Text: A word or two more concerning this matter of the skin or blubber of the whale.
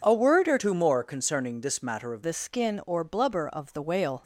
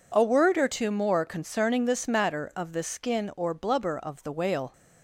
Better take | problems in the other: second | changes voice from "two" to "of"; from 0.5 to 2.2 s; 1.7 s long

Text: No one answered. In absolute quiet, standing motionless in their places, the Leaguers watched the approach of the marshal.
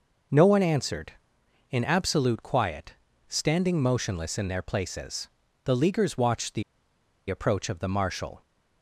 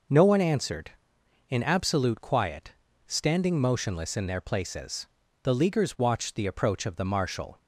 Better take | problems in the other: second | pauses between "the" and "approach"; noticeable; at 6.6 s; 0.67 s long

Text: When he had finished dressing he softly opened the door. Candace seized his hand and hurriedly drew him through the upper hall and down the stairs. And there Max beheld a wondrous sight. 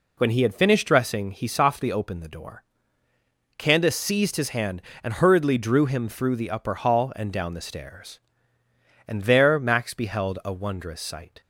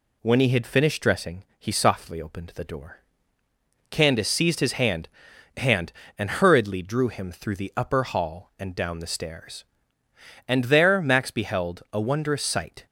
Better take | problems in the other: first | pauses between "dressing" and "he"; slight; at 1.4 s; 0.18 s long // says "hand" twice; at 5.5 s

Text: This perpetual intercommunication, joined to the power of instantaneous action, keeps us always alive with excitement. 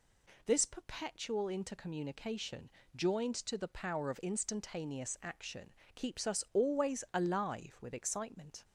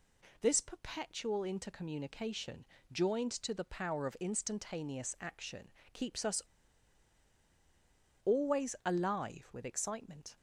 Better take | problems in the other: first | pauses between "us" and "always"; strong; at 6.4 s; 1.8 s long

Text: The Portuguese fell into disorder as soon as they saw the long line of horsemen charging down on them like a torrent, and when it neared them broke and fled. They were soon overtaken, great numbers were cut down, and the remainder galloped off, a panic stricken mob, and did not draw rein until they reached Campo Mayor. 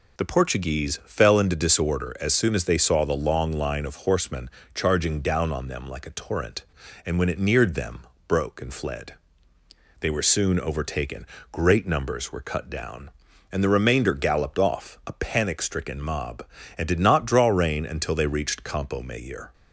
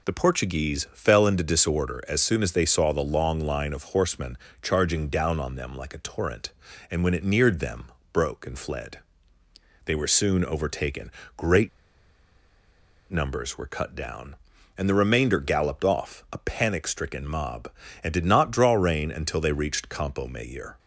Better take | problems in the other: first | pauses between "horsemen" and "charging"; slight; at 4.3 s; 0.26 s long; slight in the first // pauses between "them" and "broke"; slight; at 7.8 s; 0.26 s long; slight in the first // pauses between "great" and "numbers"; strong; at 11.6 s; 1.4 s long

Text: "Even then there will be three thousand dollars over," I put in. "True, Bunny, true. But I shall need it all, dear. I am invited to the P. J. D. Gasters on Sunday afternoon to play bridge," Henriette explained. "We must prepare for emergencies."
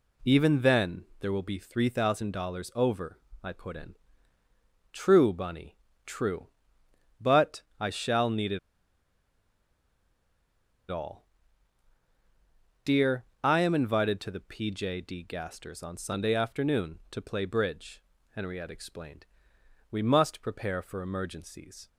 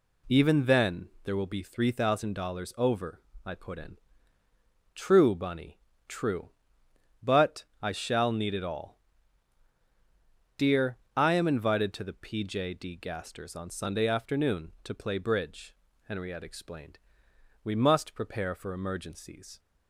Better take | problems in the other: second | pauses between "then" and "there"; slight; at 1.0 s; 0.16 s long; slight in the second // pauses between "But" and "I"; slight; at 7.6 s; 0.16 s long; slight in the second // pauses between "it" and "all"; strong; at 8.5 s; 2.3 s long

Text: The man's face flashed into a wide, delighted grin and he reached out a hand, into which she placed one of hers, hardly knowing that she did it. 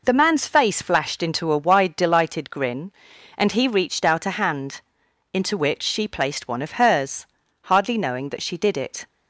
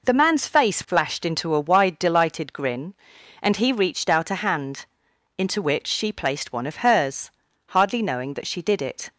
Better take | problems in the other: neither | none

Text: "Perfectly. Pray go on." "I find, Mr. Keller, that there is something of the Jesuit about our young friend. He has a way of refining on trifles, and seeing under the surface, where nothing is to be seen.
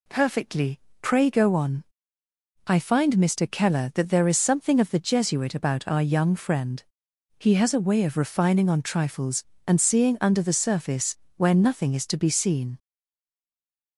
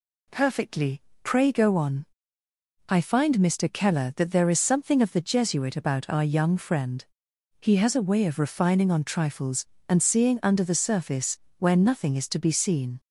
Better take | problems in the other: second | stays silent after the last word; noticeable; from 12.7 s on; 1.2 s long

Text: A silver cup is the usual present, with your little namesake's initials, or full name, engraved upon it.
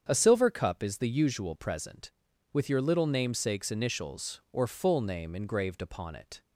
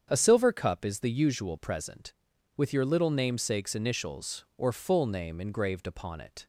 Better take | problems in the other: neither | starts louder than the rest; strong; the same in both

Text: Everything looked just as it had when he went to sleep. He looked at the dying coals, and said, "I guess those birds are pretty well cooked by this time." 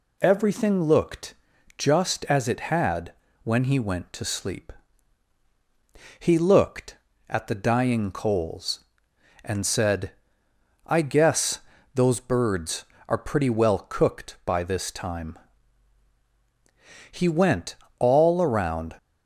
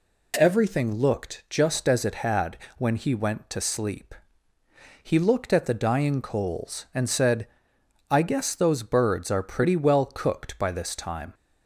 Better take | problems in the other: second | pauses between "looked" and "just"; at 1.3 s; 0.42 s long // pauses between "had" and "when"; slight; at 3.1 s; 0.30 s long; slight in the second // pauses between "guess" and "those"; at 11.5 s; 0.38 s long // goes on to say "He went all around"; strong; from 17.1 s on; 1.8 s long

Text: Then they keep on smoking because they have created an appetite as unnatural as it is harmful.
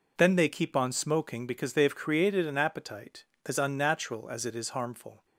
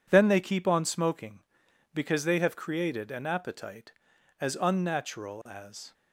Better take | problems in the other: first | stops before "it is harmful"; at 5.9 s

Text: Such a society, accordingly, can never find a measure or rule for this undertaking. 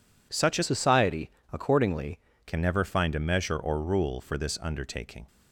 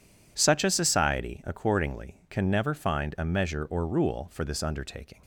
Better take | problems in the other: second | changes voice from "society" to "accordingly"; from 0.6 to 2.1 s; 1.5 s long

